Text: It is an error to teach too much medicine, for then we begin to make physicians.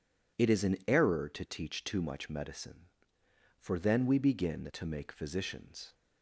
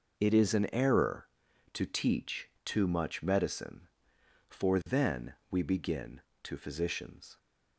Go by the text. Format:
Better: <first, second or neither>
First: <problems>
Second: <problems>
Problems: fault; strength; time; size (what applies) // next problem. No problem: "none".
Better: first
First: none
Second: pauses between "teach" and "too"; slight; at 2.4 s; 0.16 s long // pauses between "then" and "we"; slight; at 5.3 s; 0.16 s long // skips "make"; at 6.5 s